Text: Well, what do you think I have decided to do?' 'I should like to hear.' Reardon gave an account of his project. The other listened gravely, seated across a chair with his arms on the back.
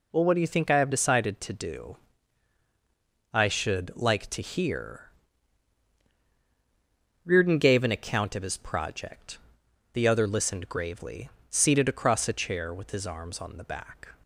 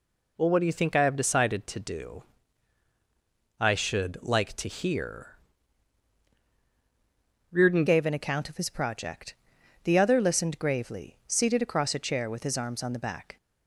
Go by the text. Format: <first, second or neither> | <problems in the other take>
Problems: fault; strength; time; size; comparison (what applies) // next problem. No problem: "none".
first | changes voice at "gave"; from 7.8 s on; 5.5 s long